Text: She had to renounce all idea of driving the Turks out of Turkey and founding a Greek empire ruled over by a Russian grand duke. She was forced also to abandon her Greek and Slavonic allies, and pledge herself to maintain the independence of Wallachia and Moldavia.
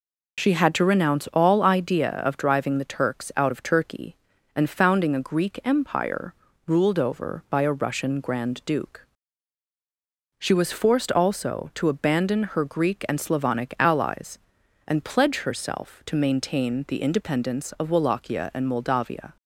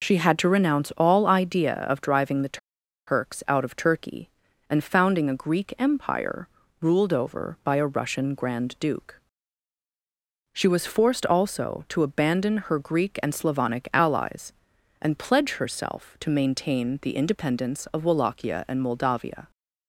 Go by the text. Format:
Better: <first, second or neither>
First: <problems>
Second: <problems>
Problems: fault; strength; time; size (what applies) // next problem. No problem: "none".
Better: first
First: pauses between "empire" and "ruled"; slight; at 6.3 s; 0.32 s long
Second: pauses between "the" and "Turks"; noticeable; at 2.5 s; 0.50 s long // pauses between "empire" and "ruled"; slight; at 6.4 s; 0.32 s long